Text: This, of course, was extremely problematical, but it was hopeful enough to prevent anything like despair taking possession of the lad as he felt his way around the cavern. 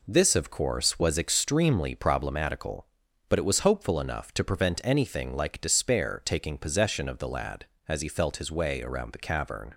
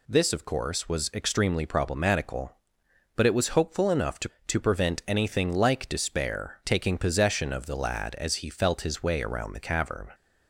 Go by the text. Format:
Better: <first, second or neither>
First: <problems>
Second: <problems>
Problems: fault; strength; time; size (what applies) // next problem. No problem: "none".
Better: first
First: none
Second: says "to" twice; at 4.4 s